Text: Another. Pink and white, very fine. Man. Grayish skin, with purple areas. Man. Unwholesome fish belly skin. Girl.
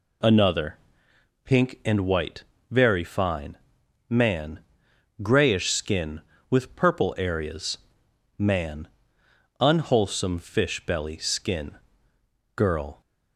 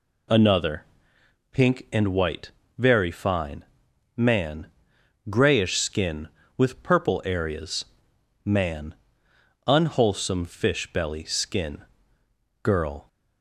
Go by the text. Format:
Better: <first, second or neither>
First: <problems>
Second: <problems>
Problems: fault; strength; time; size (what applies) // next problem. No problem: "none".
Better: neither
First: none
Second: none